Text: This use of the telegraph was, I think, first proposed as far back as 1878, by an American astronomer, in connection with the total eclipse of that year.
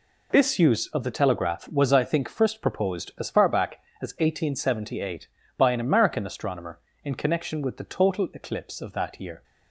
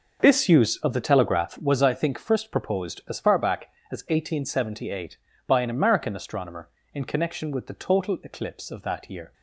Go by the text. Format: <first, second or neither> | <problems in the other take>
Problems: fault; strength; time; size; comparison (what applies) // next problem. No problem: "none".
first | starts louder than the rest; noticeable; until 1.6 s; 6 dB